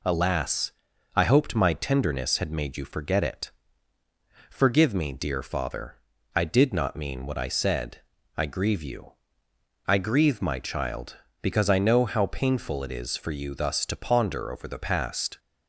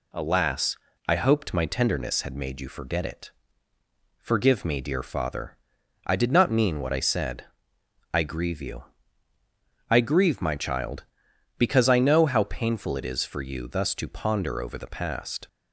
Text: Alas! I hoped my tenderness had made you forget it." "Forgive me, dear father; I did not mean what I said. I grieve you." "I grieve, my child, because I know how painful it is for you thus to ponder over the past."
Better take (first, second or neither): neither